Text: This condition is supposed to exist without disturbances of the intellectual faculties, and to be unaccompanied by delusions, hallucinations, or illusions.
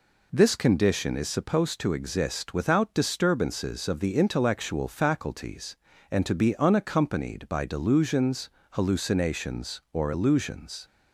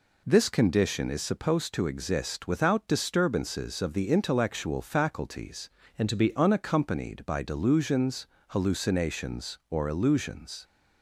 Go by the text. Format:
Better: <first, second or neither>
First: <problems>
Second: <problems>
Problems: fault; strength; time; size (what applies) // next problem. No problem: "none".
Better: first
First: none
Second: changes voice from "and" to "be"; from 5.9 to 6.3 s; 0.4 s long